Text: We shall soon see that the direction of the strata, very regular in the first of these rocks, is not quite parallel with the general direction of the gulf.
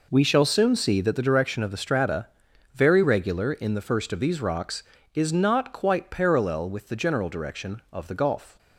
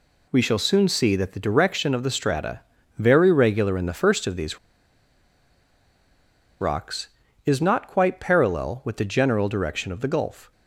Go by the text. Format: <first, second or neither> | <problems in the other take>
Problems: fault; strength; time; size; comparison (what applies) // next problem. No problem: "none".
first | pauses between "these" and "rocks"; strong; at 4.5 s; 2.0 s long